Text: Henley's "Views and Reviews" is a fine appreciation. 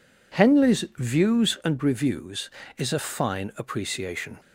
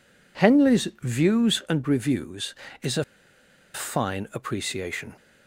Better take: first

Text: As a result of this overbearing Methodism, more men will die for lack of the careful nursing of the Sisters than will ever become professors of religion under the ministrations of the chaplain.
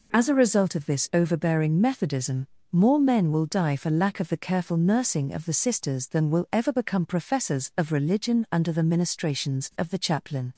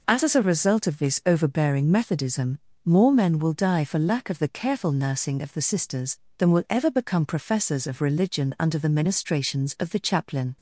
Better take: first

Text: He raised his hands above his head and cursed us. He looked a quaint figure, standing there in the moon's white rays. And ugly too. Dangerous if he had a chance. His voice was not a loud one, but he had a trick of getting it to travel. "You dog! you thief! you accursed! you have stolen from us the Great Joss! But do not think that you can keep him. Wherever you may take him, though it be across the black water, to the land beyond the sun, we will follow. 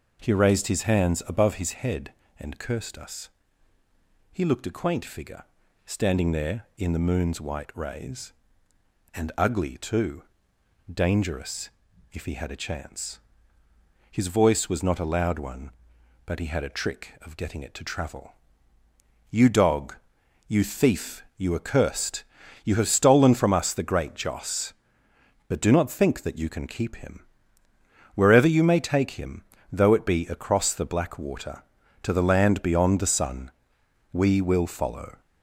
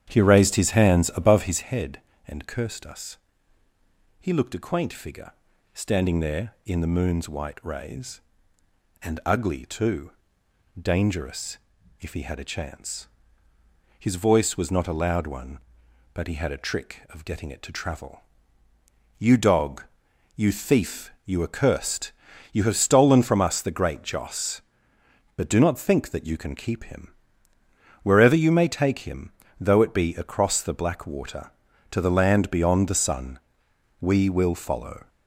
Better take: first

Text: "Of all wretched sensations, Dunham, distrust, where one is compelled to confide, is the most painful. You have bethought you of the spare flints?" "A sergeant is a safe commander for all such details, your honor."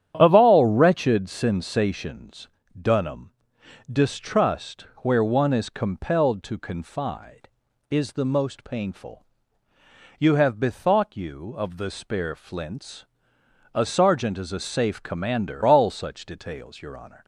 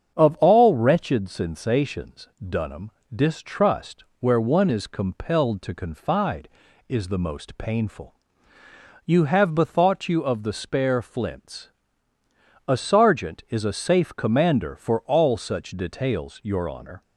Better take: second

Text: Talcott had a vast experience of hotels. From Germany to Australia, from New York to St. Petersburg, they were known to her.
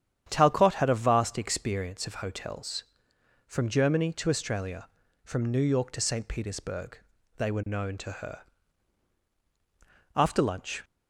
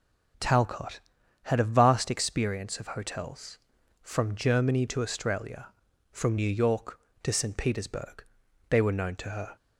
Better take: second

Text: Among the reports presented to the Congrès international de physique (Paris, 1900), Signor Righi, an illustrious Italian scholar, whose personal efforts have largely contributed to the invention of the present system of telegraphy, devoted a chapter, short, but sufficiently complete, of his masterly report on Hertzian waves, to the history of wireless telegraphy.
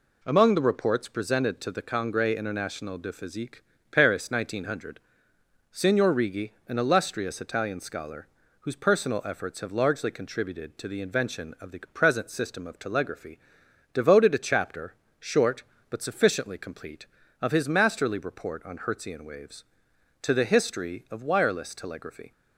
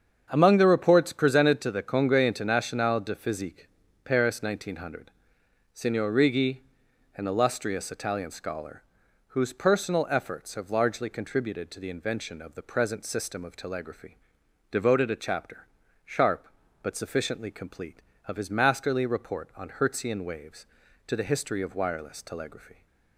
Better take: first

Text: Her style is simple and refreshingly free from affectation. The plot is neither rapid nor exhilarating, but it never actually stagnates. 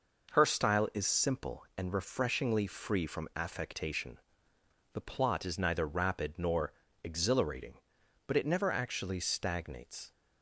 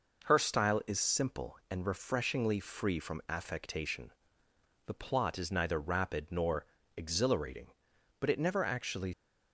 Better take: first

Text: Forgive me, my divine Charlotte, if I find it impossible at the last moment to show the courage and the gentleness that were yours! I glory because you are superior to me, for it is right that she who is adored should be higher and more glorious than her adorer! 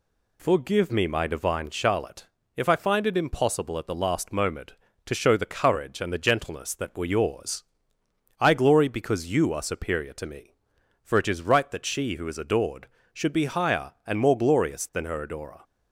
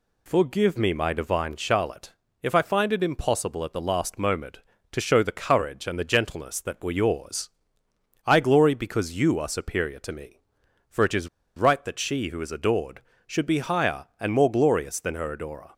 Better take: first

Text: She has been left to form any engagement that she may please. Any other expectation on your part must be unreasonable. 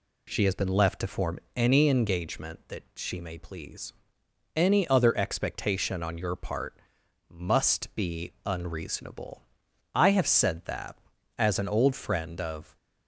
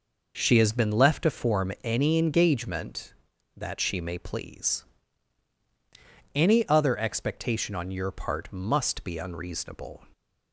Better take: second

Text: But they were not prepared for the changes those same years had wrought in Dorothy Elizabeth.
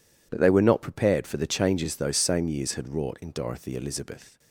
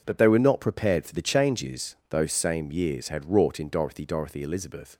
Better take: first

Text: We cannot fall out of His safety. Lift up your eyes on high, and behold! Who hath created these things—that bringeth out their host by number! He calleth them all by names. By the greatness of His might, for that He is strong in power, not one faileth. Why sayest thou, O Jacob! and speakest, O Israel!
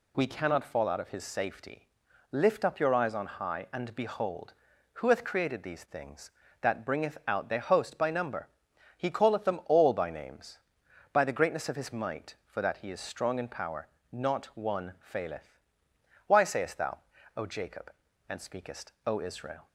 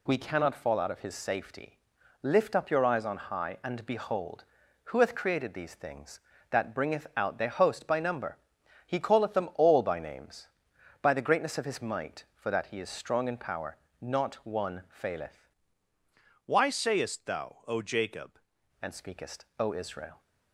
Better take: first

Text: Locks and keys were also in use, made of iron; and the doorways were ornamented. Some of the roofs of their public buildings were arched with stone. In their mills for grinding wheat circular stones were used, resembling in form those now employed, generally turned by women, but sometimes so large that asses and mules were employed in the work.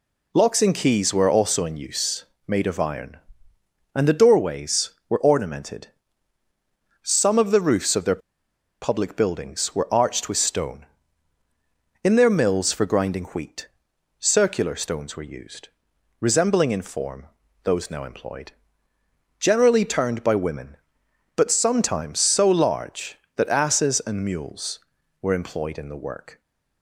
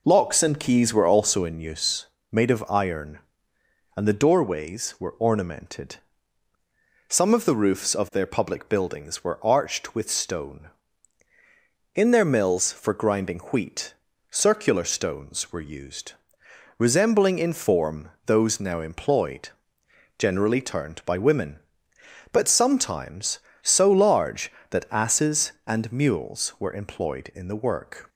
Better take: second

